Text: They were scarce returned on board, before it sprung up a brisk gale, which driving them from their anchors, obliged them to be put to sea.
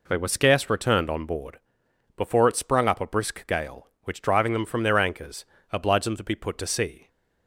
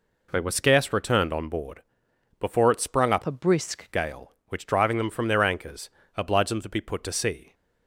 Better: first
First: none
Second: changes voice from "a" to "brisk"; from 3.2 to 3.9 s; 0.7 s long

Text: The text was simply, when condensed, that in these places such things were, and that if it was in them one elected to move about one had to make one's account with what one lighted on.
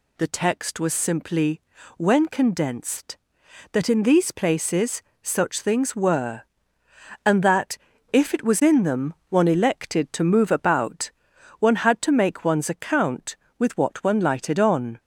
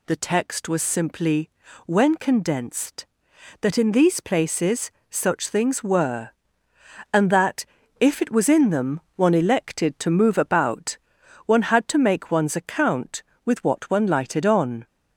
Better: neither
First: pauses between "places" and "such"; slight; at 5.0 s; 0.20 s long // pauses between "that" and "if"; slight; at 7.7 s; 0.34 s long // pauses between "them" and "one"; slight; at 9.1 s; 0.16 s long // pauses between "about" and "one"; noticeable; at 11.1 s; 0.48 s long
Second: pauses between "places" and "such"; slight; at 4.9 s; 0.18 s long // pauses between "that" and "if"; slight; at 7.6 s; 0.34 s long // pauses between "them" and "one"; slight; at 8.9 s; 0.16 s long // pauses between "about" and "one"; noticeable; at 10.9 s; 0.48 s long

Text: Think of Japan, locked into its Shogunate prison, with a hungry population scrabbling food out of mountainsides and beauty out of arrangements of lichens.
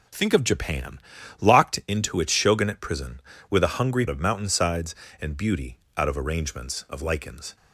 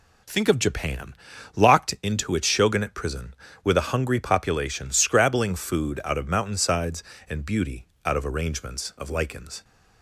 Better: second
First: skips "population scrabbling food out"; at 4.0 s // pauses between "beauty" and "out"; slight; at 5.7 s; 0.20 s long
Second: pauses between "beauty" and "out"; slight; at 7.8 s; 0.20 s long

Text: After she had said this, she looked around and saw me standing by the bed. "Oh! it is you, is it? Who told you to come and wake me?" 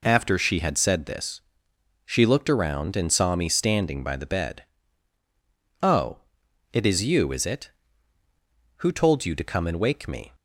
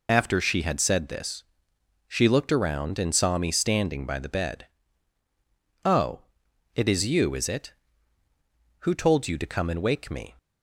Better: first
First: none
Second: loses the start of "After"; at 0.0 s; 40 ms

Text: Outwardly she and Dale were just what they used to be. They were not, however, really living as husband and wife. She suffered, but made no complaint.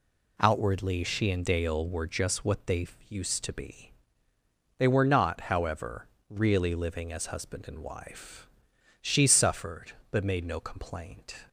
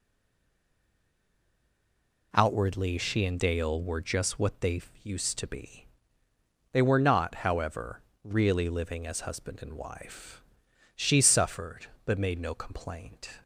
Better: first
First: pauses between "they" and "used"; slight; at 2.8 s; 0.22 s long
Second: stays silent before the first word; until 2.3 s; 2.3 s long // pauses between "they" and "used"; slight; at 4.8 s; 0.22 s long

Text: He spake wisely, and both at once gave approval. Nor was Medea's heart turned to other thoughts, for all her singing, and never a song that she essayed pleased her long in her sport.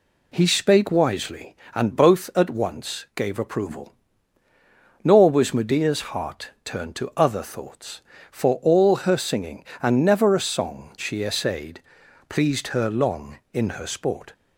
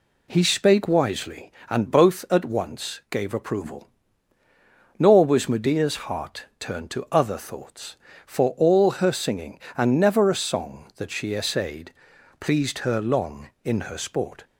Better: second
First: pauses between "heart" and "turned"; slight; at 6.4 s; 0.16 s long // skips "that"; at 10.9 s // pauses between "essayed" and "pleased"; noticeable; at 11.8 s; 0.46 s long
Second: pauses between "heart" and "turned"; slight; at 6.4 s; 0.16 s long // pauses between "essayed" and "pleased"; noticeable; at 11.9 s; 0.46 s long

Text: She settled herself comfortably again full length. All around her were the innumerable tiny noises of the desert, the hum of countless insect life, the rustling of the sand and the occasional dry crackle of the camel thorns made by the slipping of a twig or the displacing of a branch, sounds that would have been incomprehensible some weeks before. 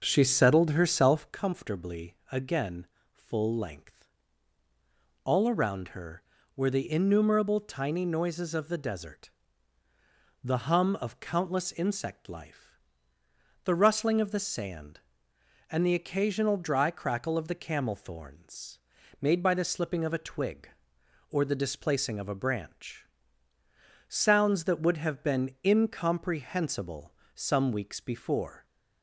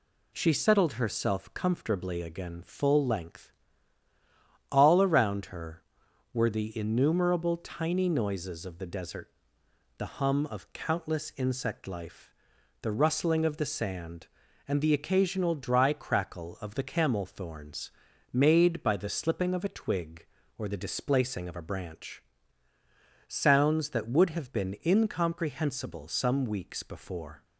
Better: second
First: starts louder than the rest; noticeable; until 1.3 s; 6 dB // pauses between "again" and "full"; slight; at 2.8 s; 0.26 s long // pauses between "thorns" and "made"; at 18.7 s; 0.42 s long // pauses between "incomprehensible" and "some"; slight; at 27.1 s; 0.22 s long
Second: pauses between "thorns" and "made"; at 17.9 s; 0.40 s long

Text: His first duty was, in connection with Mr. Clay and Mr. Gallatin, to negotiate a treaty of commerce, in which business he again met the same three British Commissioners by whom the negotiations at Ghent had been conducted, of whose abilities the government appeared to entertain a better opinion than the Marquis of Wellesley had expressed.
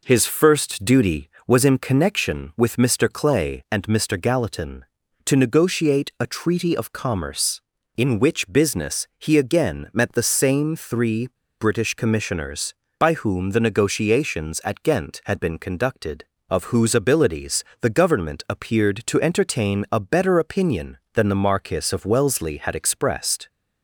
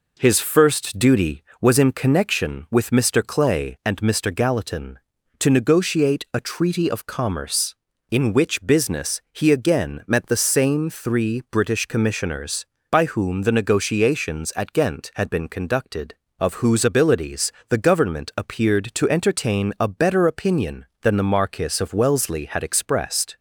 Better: second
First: pauses between "three" and "British"; slight; at 11.2 s; 0.32 s long // pauses between "abilities" and "the"; slight; at 17.6 s; 0.18 s long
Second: pauses between "abilities" and "the"; slight; at 17.5 s; 0.18 s long

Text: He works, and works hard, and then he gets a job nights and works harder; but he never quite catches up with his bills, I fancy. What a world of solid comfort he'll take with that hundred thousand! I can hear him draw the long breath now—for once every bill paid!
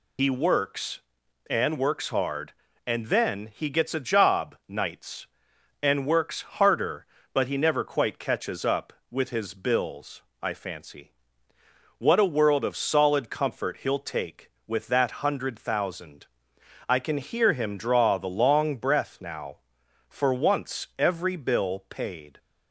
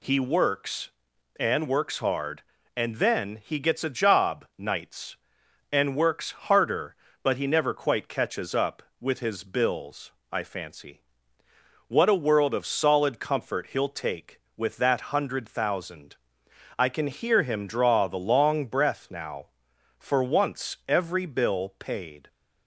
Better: second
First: loses the start of "He"; at 0.1 s; 70 ms // pauses between "works" and "harder"; slight; at 6.4 s; 0.20 s long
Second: pauses between "works" and "harder"; slight; at 6.3 s; 0.20 s long

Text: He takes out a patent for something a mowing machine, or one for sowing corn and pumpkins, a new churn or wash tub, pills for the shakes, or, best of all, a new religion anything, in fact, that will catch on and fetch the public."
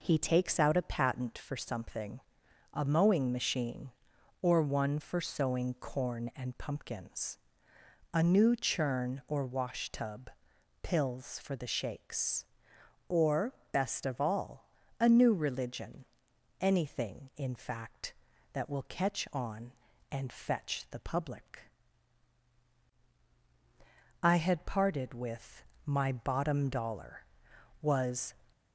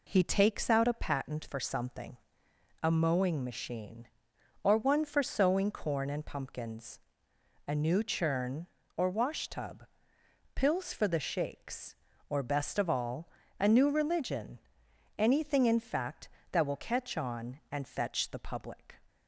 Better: second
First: pauses between "something" and "a"; noticeable; at 2.1 s; 0.54 s long // pauses between "religion" and "anything"; noticeable; at 16.0 s; 0.56 s long // goes on to say "I had parted with my bottom dollar was"; strong; from 24.2 s on; 4.1 s long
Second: pauses between "something" and "a"; noticeable; at 2.1 s; 0.62 s long // pauses between "religion" and "anything"; noticeable; at 14.5 s; 0.58 s long

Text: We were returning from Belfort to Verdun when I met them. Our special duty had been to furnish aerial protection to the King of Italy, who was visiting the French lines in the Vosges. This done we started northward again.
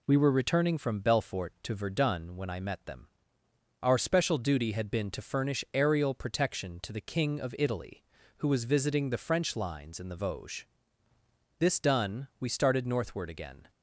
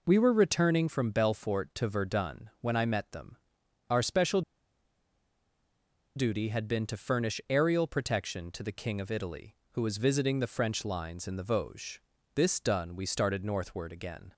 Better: first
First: none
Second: pauses between "special" and "duty"; strong; at 4.4 s; 1.7 s long

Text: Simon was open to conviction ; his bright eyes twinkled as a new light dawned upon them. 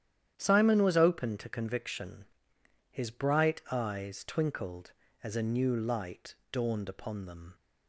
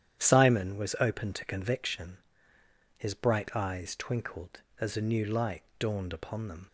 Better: neither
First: starts louder than the rest; strong; until 1.3 s; 10.5 dB // pauses between "light" and "dawned"; slight; at 6.3 s; 0.16 s long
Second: starts louder than the rest; strong; until 1.2 s; 10 dB // pauses between "light" and "dawned"; slight; at 5.6 s; 0.16 s long

